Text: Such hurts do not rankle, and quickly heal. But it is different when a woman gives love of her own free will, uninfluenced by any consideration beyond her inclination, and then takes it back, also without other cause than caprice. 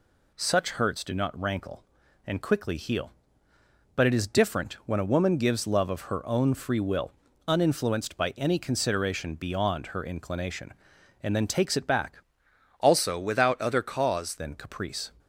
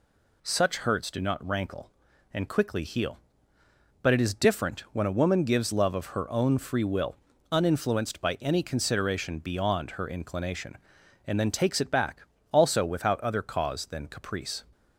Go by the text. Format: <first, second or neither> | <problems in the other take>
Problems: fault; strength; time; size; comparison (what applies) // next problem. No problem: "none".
second | changes voice from "also" to "cause"; from 12.7 to 14.3 s; 1.6 s long